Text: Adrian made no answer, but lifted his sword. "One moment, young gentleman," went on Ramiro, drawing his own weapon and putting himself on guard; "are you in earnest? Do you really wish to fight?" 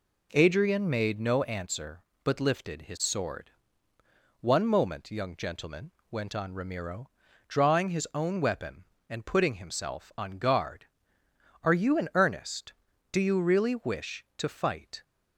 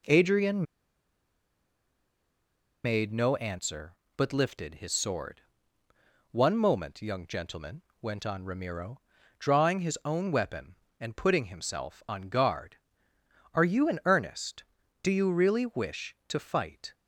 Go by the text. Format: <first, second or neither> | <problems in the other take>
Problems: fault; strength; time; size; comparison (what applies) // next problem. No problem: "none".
first | pauses between "Adrian" and "made"; strong; at 0.6 s; 2.2 s long